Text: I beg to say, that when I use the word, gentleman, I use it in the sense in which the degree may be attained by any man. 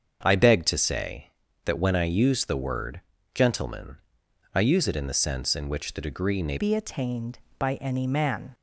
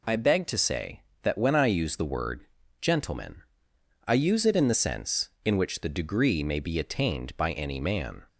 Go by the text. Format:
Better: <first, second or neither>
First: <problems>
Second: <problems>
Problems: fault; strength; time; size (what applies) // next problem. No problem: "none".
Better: second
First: starts louder than the rest; until 1.2 s; 7 dB // changes voice at "be"; from 6.5 s on; 2.0 s long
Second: none